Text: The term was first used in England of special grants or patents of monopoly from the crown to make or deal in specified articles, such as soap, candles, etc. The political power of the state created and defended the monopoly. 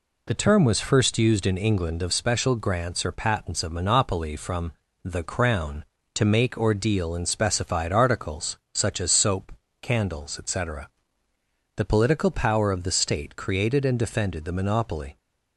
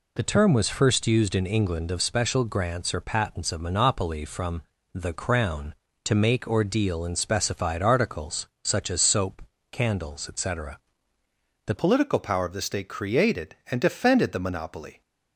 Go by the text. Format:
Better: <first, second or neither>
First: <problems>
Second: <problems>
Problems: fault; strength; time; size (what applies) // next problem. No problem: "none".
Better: first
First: pauses between "from" and "the"; slight; at 4.7 s; 0.28 s long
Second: pauses between "from" and "the"; slight; at 4.6 s; 0.28 s long // changes voice at "political"; from 11.7 s on; 3.3 s long